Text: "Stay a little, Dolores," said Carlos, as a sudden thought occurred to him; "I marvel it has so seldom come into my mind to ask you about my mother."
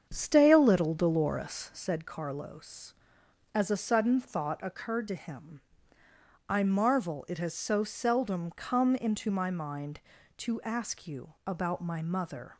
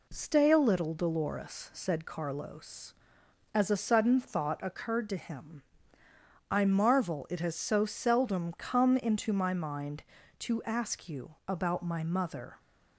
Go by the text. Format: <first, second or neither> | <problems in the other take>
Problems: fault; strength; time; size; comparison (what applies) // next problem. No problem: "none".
second | starts louder than the rest; strong; until 1.8 s; 7.5 dB